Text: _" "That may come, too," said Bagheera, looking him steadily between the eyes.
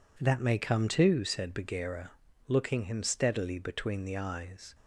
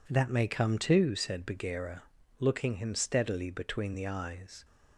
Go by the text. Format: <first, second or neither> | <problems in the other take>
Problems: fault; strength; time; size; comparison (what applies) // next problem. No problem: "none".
neither | none